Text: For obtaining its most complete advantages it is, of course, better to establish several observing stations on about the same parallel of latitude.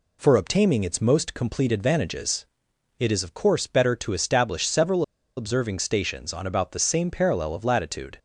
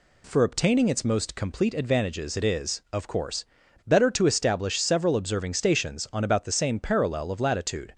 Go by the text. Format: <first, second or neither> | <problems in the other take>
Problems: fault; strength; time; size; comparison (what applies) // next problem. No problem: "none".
second | pauses between "advantages" and "it"; noticeable; at 2.4 s; 0.54 s long // pauses between "several" and "observing"; slight; at 5.0 s; 0.35 s long